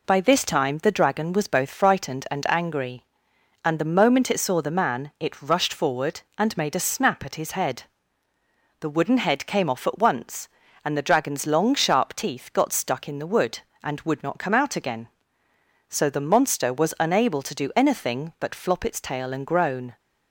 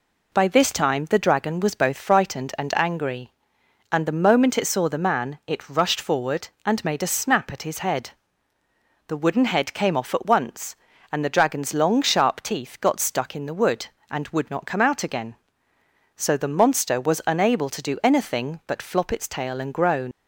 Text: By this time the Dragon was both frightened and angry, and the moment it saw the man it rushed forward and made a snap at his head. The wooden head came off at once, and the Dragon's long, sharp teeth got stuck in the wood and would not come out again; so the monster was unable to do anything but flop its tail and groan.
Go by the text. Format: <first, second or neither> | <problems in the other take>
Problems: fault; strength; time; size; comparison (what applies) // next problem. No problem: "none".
first | leaves "groan" unfinished; at 20.1 s; 115 ms